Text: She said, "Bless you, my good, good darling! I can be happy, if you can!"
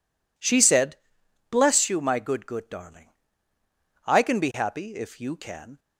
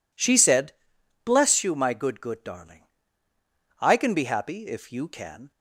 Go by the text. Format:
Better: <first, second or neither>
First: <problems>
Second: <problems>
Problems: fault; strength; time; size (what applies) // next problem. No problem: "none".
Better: neither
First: none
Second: none